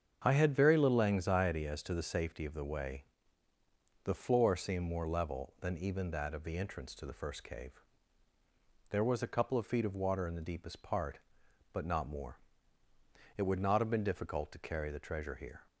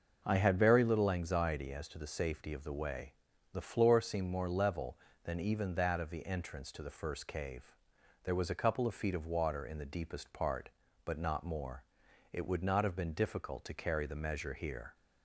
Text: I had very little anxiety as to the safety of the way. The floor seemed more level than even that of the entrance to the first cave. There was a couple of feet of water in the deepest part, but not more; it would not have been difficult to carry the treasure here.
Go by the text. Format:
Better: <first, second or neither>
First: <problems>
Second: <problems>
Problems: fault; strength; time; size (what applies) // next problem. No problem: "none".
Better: first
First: starts louder than the rest; strong; until 1.2 s; 7.5 dB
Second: starts louder than the rest; noticeable; until 1.2 s; 6 dB // says "measure" for "treasure"; at 14.1 s